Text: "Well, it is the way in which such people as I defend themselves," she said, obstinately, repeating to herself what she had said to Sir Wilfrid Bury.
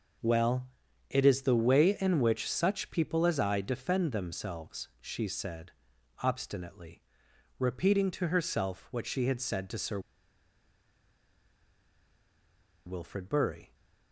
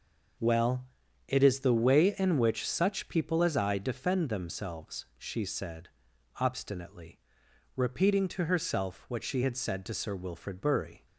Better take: second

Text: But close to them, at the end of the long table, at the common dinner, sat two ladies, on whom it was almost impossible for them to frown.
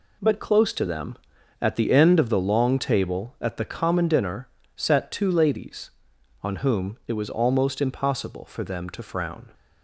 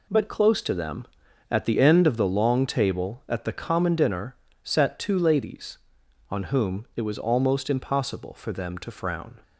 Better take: neither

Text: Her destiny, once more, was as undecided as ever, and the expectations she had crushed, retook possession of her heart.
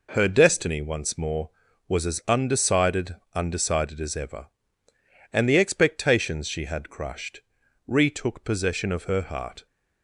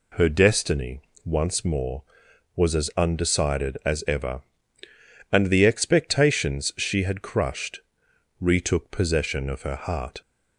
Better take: second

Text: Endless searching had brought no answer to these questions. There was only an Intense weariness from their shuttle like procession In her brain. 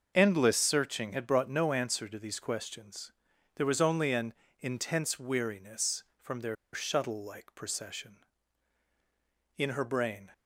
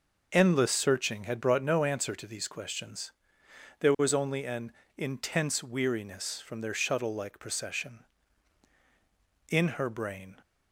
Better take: second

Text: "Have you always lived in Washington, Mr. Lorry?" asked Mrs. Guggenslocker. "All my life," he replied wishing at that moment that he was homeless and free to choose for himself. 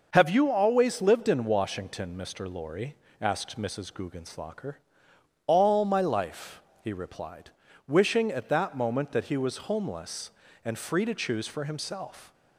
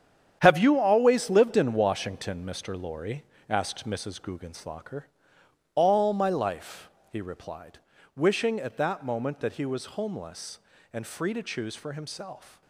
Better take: first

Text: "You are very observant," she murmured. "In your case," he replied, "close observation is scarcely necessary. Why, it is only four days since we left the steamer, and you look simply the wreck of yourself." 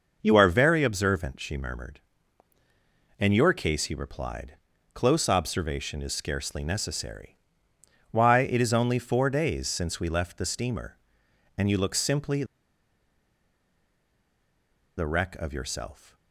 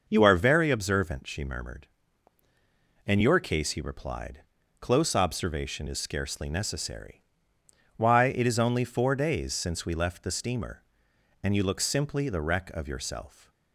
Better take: second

